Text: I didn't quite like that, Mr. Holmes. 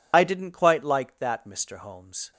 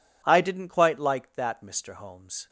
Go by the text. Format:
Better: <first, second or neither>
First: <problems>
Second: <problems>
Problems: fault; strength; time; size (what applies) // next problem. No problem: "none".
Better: second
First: loses the start of "I"; at 0.1 s; 65 ms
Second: none